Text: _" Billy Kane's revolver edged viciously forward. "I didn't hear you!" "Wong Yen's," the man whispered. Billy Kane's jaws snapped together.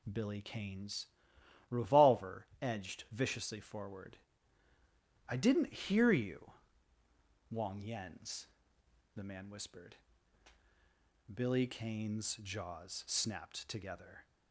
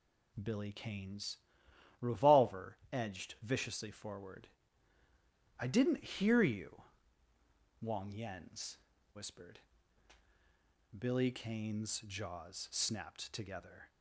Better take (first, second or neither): first